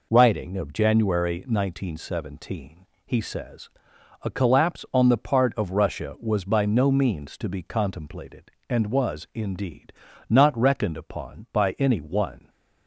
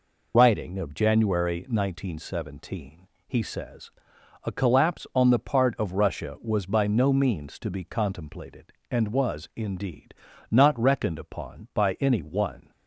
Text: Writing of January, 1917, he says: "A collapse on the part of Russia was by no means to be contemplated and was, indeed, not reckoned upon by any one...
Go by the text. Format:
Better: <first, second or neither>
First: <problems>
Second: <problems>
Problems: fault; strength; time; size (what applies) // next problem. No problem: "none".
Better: first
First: none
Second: loses the start of "Writing"; at 0.3 s; 25 ms